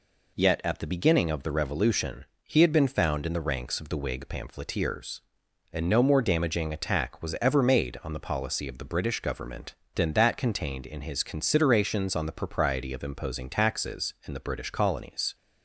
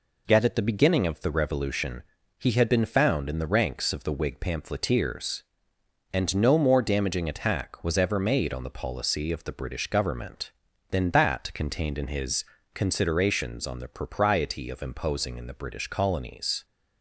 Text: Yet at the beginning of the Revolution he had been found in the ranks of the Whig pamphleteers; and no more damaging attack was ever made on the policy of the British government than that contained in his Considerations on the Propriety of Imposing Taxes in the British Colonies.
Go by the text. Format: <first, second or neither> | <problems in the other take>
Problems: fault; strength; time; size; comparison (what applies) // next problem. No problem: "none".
first | pauses between "Revolution" and "he"; slight; at 2.0 s; 0.34 s long; slight in the first // pauses between "his" and "Considerations"; slight; at 12.4 s; 0.30 s long // skips "Taxes"; at 15.3 s